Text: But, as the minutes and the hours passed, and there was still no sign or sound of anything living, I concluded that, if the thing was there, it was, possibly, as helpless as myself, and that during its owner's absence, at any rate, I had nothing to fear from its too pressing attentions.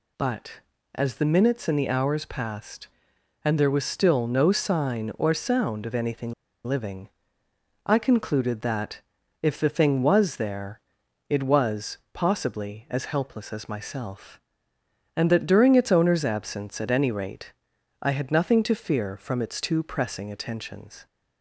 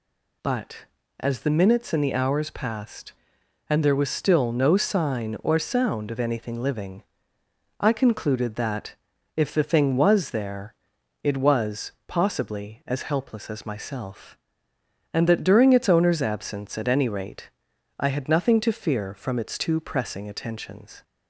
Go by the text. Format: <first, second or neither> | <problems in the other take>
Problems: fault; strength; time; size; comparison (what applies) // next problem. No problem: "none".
second | pauses between "anything" and "living"; slight; at 6.3 s; 0.33 s long